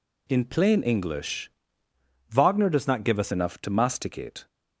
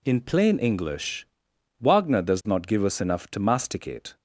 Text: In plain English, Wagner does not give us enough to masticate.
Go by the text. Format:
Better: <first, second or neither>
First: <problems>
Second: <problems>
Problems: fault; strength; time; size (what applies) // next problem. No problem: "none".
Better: second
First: changes voice from "Wagner" to "us"; from 2.2 to 3.3 s; 1.1 s long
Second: none